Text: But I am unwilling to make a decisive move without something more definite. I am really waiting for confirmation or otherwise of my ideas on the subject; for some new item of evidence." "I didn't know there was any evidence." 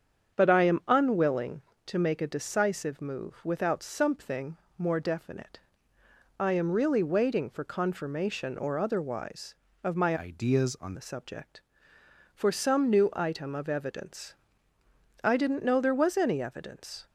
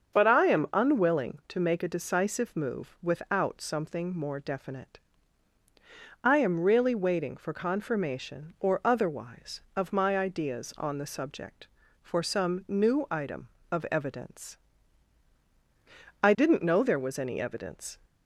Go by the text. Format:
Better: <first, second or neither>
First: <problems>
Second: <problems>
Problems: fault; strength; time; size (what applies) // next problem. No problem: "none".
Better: second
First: starts louder than the rest; strong; until 1.4 s; 7.5 dB // pauses between "something" and "more"; slight; at 4.5 s; 0.20 s long // changes voice from "ideas" to "on"; from 10.1 to 10.9 s; 0.8 s long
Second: starts louder than the rest; until 1.1 s; 7 dB